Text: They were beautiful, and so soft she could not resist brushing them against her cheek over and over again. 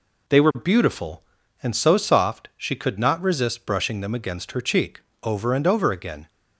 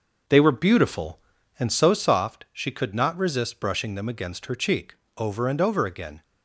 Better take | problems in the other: first | starts louder than the rest; noticeable; until 2.0 s; 6 dB // pauses between "cheek" and "over"; slight; at 4.9 s; 0.22 s long; slight in the first

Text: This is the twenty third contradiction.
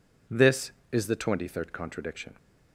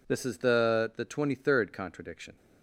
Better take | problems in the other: first | says "the" twice; at 0.9 s

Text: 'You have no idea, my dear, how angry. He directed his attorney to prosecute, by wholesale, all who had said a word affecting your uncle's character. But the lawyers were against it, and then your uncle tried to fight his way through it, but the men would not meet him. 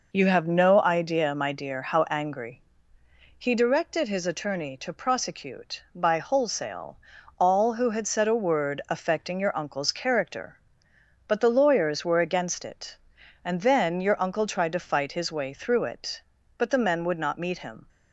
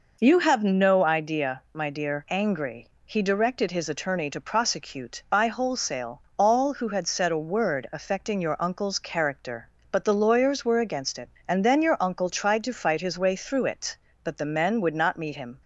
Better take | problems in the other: first | skips "how"; at 2.2 s

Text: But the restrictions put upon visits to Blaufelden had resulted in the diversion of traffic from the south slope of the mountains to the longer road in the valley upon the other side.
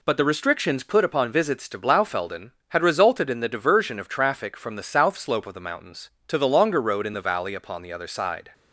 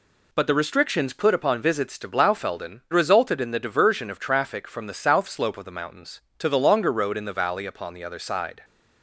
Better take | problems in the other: first | skips "had"; at 2.8 s

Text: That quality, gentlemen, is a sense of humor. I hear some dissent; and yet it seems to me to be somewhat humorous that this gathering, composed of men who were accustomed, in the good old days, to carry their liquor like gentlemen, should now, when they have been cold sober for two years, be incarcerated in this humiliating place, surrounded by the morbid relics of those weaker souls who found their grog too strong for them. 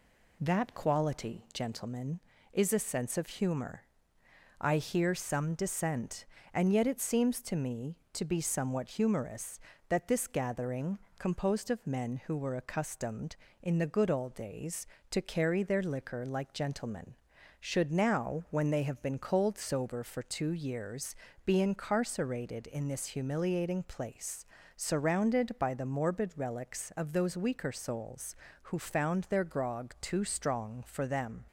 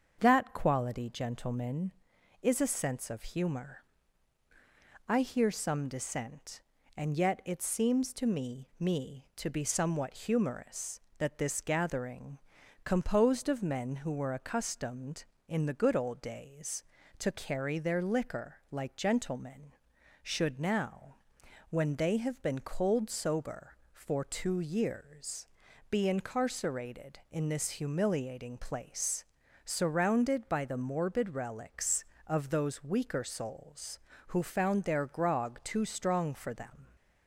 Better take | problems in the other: first | starts louder than the rest; until 1.2 s; 6.5 dB // says "me" twice; at 8.7 s

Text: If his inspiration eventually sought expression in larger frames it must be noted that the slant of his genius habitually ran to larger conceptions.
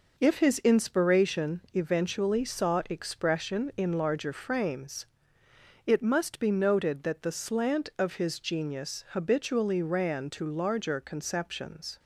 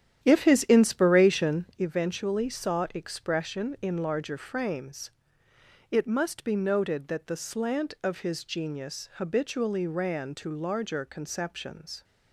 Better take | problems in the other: first | starts louder than the rest; strong; until 1.9 s; 10 dB // pauses between "frames" and "it"; noticeable; at 5.0 s; 0.80 s long; noticeable in the first

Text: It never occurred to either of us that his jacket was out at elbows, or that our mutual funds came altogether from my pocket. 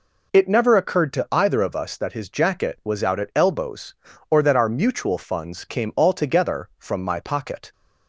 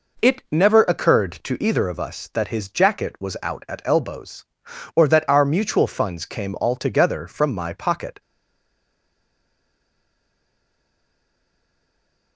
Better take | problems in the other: first | stays silent after the last word; strong; from 8.2 s on; 4.1 s long

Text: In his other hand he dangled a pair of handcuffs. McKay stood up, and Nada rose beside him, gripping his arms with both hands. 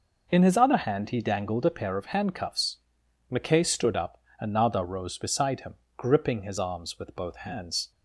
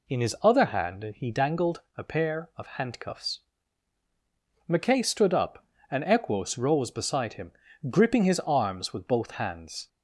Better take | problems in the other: first | pauses between "dangled" and "a"; slight; at 1.8 s; 0.16 s long // says "Equos" for "Nada"; at 6.0 s

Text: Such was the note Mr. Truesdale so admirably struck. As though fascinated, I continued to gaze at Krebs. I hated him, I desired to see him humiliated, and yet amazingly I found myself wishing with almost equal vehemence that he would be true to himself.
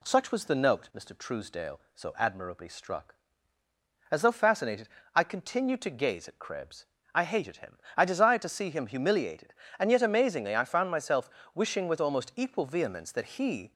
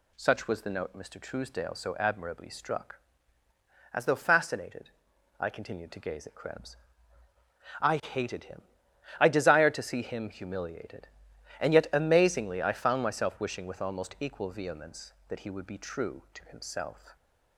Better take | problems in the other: second | pauses between "myself" and "wishing"; slight; at 11.3 s; 0.24 s long // stops before "would be true to himself"; at 13.6 s

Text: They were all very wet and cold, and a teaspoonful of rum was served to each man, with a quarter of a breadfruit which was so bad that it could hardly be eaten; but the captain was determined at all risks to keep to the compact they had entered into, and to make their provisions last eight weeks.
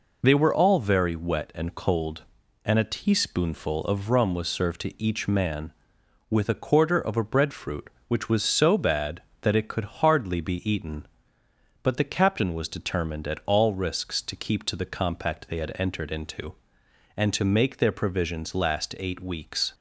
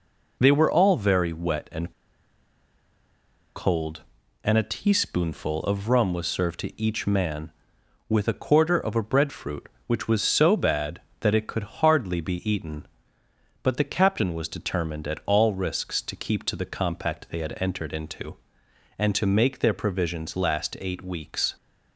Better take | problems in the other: first | pauses between "and" and "cold"; strong; at 1.9 s; 1.6 s long

